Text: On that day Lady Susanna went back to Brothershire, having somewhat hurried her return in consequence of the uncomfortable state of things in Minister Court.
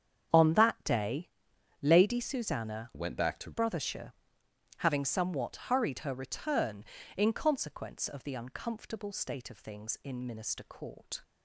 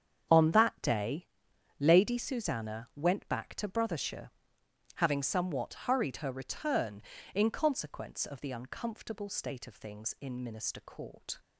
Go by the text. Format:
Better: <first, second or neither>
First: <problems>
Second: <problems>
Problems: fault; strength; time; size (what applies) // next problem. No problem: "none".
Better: second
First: starts louder than the rest; strong; until 1.9 s; 8.5 dB // pauses between "day" and "Lady"; noticeable; at 1.2 s; 0.54 s long // changes voice from "went" to "to"; from 2.9 to 3.5 s; 0.6 s long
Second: starts louder than the rest; strong; until 1.9 s; 8.5 dB // pauses between "day" and "Lady"; noticeable; at 1.2 s; 0.54 s long